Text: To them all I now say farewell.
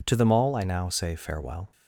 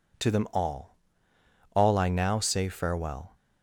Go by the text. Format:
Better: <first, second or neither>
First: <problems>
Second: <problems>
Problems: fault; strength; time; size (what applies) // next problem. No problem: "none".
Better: first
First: none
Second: says "all" twice; at 1.7 s